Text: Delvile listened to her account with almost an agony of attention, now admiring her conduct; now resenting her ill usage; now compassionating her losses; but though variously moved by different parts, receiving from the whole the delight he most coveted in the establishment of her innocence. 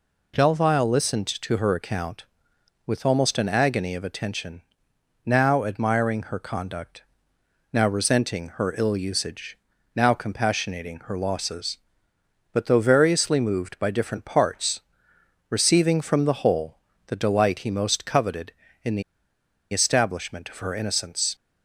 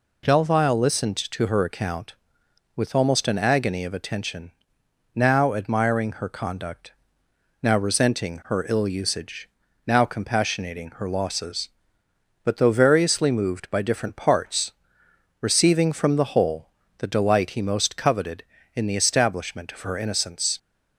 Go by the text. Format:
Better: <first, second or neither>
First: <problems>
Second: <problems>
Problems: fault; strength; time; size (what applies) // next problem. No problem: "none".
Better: second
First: pauses between "whole" and "the"; slight; at 16.7 s; 0.28 s long // pauses between "the" and "establishment"; noticeable; at 19.0 s; 0.70 s long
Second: pauses between "whole" and "the"; slight; at 16.6 s; 0.28 s long